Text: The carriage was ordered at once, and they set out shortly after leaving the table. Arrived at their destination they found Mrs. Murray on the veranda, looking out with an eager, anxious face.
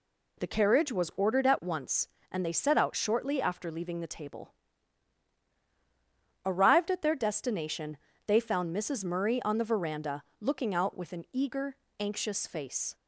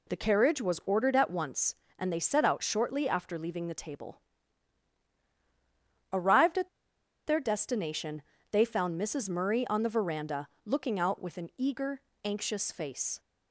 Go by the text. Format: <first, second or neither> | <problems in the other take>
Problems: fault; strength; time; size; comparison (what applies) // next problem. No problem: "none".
first | pauses between "at" and "their"; noticeable; at 6.6 s; 0.58 s long // pauses between "destination" and "they"; slight; at 8.2 s; 0.30 s long; slight in the first